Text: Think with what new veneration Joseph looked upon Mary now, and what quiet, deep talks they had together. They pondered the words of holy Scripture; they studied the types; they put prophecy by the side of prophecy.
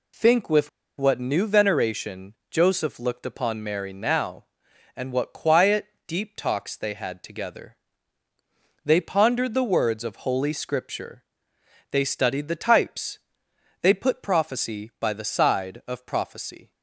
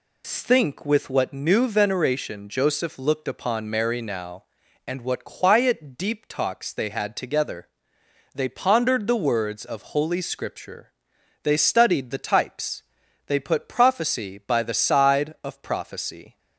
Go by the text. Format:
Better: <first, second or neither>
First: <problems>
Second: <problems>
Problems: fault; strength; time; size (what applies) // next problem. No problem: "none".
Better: second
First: pauses between "with" and "what"; slight; at 0.6 s; 0.29 s long // pauses between "veneration" and "Joseph"; slight; at 2.3 s; 0.18 s long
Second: none